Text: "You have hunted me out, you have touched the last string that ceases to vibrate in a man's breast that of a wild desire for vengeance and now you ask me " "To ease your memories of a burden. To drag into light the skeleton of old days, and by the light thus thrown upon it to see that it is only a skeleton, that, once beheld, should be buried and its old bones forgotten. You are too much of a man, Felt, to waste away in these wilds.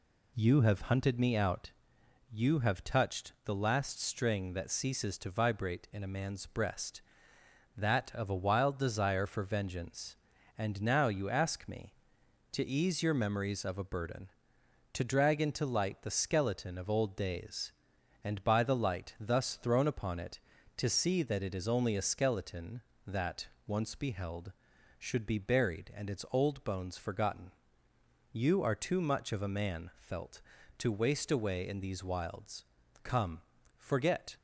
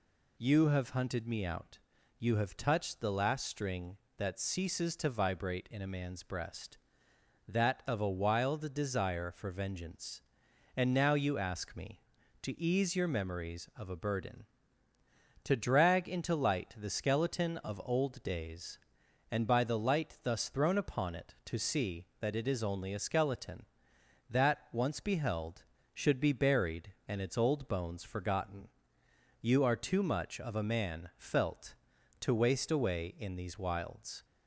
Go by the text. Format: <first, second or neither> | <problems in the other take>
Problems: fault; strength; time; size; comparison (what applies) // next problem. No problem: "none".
second | goes on to say "Come forget"; from 33.0 s on; 1.3 s long